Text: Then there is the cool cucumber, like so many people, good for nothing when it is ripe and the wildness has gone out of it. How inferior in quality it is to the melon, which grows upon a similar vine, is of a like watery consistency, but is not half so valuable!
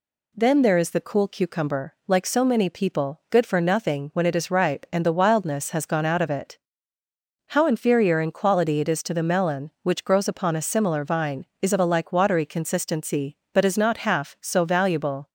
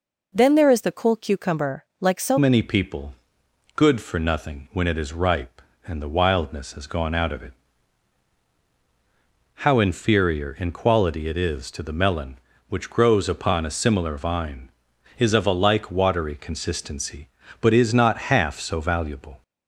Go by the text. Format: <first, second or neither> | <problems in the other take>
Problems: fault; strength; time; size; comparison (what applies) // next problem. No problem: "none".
first | changes voice at "many"; from 2.3 s on; 17.1 s long